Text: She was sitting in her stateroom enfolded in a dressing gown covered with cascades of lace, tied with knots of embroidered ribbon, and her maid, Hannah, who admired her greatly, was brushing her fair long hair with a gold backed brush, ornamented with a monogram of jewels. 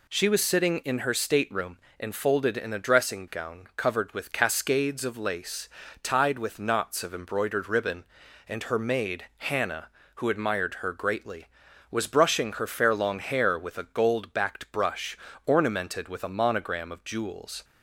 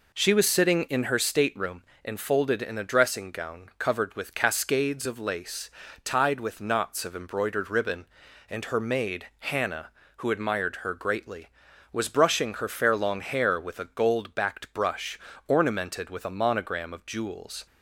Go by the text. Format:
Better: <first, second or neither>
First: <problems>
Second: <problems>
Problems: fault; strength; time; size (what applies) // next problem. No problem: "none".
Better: first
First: pauses between "stateroom" and "enfolded"; slight; at 1.7 s; 0.20 s long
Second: starts louder than the rest; noticeable; until 1.5 s; 4 dB // pauses between "stateroom" and "enfolded"; slight; at 1.8 s; 0.20 s long